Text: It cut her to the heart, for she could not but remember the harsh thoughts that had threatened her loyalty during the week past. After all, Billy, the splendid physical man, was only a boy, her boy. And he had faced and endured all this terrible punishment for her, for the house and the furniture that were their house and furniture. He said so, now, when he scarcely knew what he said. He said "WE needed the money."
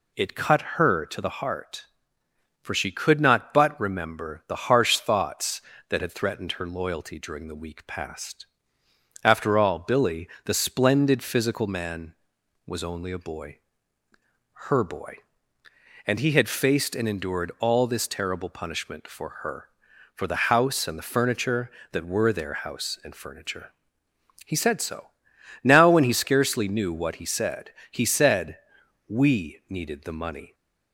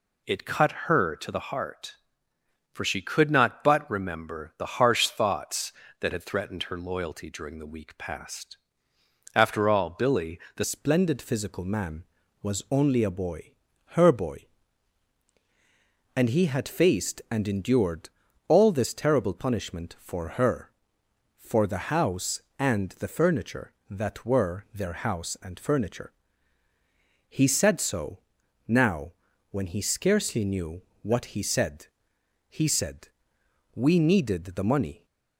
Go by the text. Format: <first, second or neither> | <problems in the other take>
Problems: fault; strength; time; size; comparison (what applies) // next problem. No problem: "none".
first | changes voice at "splendid"; from 10.6 s on; 24.4 s long // pauses between "endured" and "all"; at 18.0 s; 0.38 s long // pauses between "knew" and "what"; slight; at 30.8 s; 0.22 s long // pauses between "said" and "WE"; noticeable; at 33.0 s; 0.66 s long; noticeable in the first